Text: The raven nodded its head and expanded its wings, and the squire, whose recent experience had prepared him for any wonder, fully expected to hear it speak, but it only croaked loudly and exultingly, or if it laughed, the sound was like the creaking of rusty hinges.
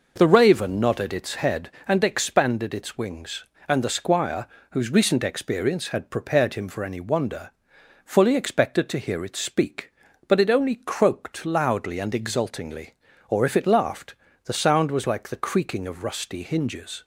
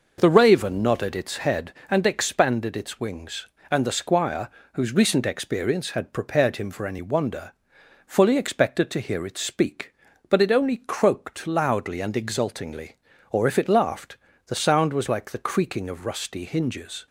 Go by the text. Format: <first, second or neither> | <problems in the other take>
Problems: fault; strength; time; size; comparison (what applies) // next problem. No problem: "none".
neither | none